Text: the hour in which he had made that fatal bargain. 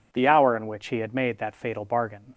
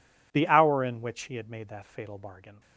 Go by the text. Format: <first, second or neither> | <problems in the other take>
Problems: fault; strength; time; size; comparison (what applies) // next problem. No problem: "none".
neither | none